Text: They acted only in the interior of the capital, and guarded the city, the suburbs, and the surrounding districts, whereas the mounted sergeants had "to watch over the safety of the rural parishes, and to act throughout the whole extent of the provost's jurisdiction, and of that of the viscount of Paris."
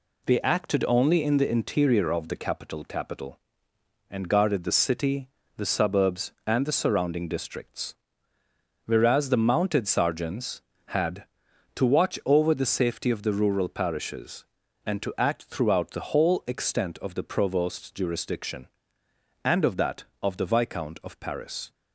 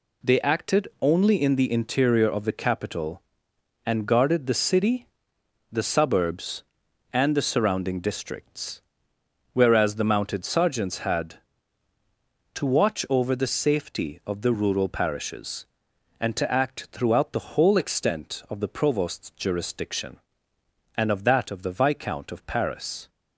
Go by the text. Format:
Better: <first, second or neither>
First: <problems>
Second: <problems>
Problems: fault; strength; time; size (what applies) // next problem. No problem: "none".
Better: second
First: says "capital" twice; at 2.8 s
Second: none